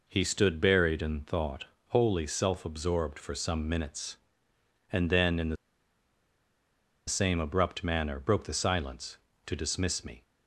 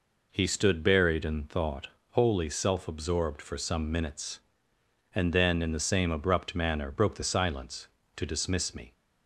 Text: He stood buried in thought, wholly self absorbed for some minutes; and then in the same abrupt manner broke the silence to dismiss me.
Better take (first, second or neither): second